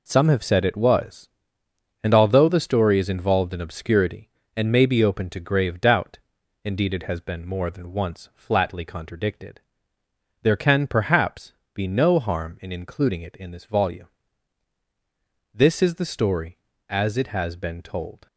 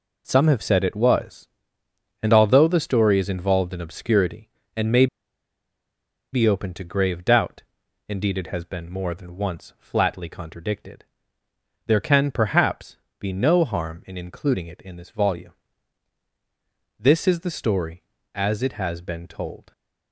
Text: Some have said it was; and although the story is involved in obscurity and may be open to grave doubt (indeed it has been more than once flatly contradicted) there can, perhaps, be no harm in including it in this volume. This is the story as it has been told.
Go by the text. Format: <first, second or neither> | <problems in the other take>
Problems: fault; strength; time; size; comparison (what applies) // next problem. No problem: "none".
first | pauses between "may" and "be"; strong; at 5.0 s; 1.2 s long